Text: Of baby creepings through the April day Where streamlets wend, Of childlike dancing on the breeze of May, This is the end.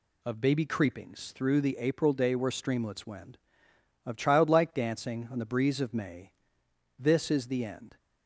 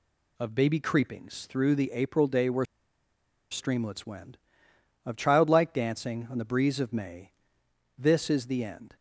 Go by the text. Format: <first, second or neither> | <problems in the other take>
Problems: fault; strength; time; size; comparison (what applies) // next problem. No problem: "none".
first | pauses between "Where" and "streamlets"; noticeable; at 2.6 s; 0.85 s long